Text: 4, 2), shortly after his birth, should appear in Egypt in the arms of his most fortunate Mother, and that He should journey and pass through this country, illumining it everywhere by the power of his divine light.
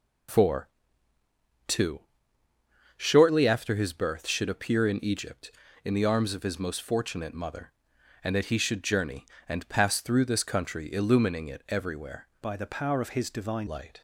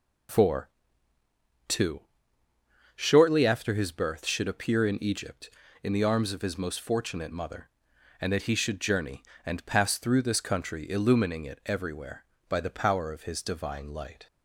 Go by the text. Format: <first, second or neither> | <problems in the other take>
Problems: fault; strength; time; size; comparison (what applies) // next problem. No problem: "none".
second | changes voice from "by" to "divine"; from 12.4 to 13.6 s; 1.2 s long